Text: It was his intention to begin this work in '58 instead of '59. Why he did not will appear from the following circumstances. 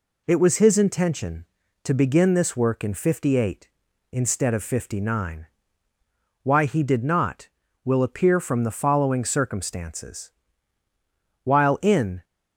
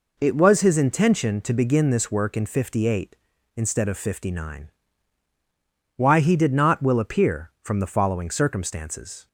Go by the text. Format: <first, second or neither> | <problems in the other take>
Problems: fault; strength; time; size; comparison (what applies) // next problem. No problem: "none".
second | goes on to say "While in"; noticeable; from 11.4 s on; 0.80 s long